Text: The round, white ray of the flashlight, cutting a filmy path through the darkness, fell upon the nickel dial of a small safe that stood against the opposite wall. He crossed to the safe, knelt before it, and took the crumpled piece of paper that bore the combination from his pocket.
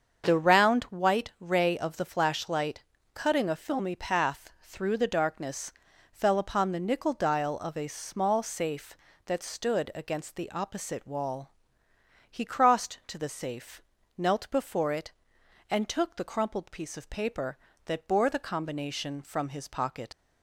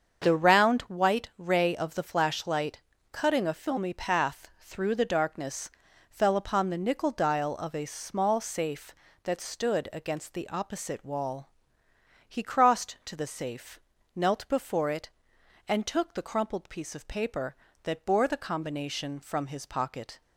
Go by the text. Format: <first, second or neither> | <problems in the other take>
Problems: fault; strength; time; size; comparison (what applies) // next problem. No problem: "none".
second | starts louder than the rest; until 1.2 s; 7 dB; also in the second // leaves "pocket" unfinished; at 20.1 s; 100 ms